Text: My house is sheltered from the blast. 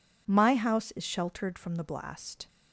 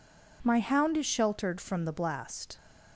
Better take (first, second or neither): first